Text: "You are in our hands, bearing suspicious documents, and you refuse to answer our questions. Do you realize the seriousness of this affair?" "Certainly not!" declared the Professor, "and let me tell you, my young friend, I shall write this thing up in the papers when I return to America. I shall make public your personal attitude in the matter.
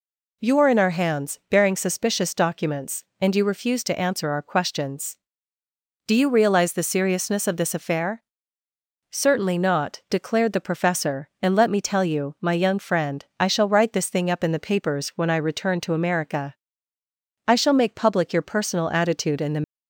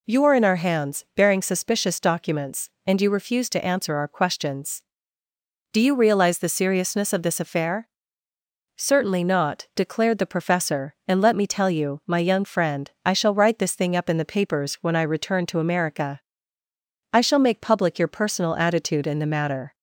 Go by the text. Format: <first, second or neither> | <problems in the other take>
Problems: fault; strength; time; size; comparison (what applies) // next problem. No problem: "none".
second | stops before "matter"; at 19.6 s